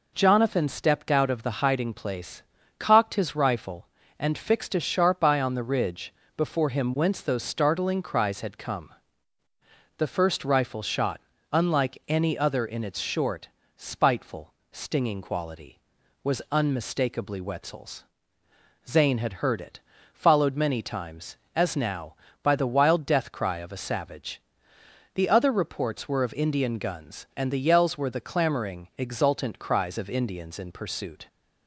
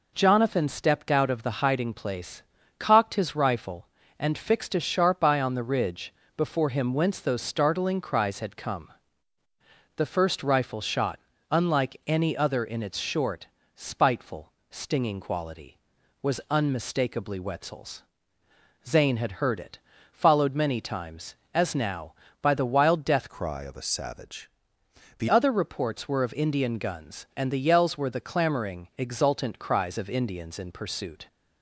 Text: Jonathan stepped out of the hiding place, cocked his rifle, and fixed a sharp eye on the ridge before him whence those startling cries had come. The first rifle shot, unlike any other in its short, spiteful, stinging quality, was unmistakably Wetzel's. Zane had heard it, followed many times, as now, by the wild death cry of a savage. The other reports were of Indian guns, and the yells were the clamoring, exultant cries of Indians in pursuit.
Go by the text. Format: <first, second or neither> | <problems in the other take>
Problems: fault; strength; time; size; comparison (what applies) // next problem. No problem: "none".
first | pauses between "ridge" and "before"; slight; at 6.1 s; 0.22 s long; slight in the first // changes voice from "cry" to "The"; from 23.2 to 25.2 s; 2.0 s long